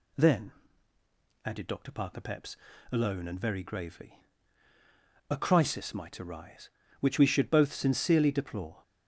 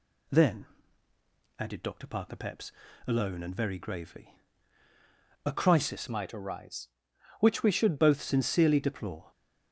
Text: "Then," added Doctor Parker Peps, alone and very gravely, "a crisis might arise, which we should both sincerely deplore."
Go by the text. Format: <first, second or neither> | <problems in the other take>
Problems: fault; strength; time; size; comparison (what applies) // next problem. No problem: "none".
first | changes voice from "might" to "should"; from 6.0 to 7.9 s; 1.9 s long